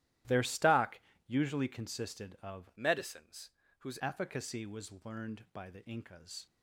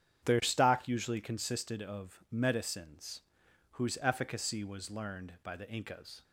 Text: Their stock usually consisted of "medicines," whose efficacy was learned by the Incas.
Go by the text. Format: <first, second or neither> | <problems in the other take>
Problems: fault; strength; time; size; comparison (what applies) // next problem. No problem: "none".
second | starts louder than the rest; strong; until 1.5 s; 13.5 dB; strong in the second // pauses between "stock" and "usually"; slight; at 0.9 s; 0.30 s long // changes voice from "medicines" to "whose"; from 2.7 to 3.9 s; 1.2 s long